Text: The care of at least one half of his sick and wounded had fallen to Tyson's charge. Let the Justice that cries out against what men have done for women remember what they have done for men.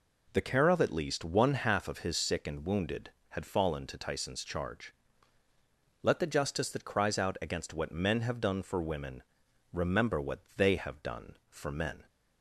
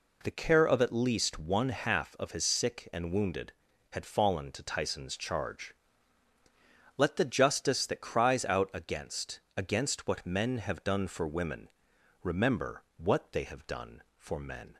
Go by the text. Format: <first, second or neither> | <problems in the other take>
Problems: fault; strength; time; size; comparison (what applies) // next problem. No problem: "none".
first | says "against" twice; at 9.5 s // pauses between "women" and "remember"; noticeable; at 11.6 s; 0.54 s long; noticeable in the first